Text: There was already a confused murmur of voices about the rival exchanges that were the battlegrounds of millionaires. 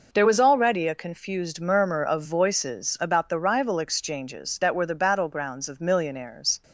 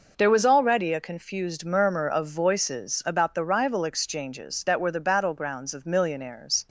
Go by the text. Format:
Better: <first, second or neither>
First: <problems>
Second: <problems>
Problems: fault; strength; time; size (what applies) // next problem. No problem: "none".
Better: neither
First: none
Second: none